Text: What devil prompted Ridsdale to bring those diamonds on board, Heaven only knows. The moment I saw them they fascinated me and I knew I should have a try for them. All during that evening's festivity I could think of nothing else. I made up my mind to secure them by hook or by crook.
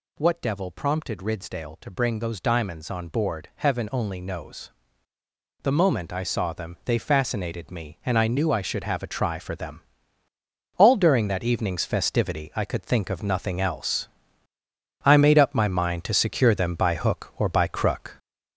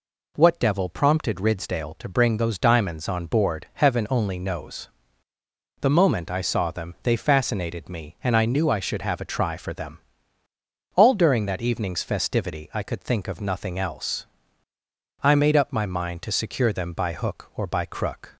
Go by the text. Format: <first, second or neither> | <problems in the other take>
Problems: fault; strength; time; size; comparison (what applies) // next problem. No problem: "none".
second | gets louder; noticeable; throughout; 5 dB